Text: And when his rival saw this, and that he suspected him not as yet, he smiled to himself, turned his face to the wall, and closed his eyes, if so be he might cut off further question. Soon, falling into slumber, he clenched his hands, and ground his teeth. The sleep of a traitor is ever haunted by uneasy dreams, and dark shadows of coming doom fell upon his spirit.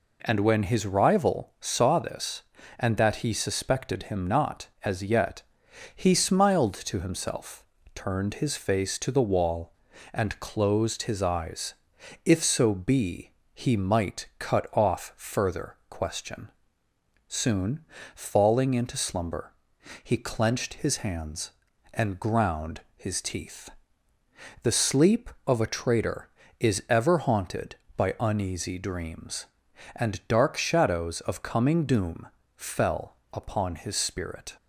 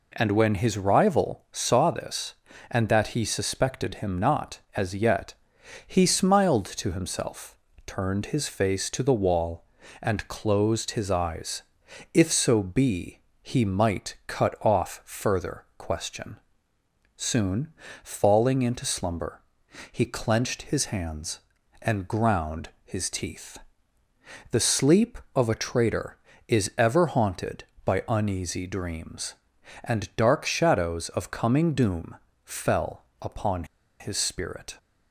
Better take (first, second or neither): first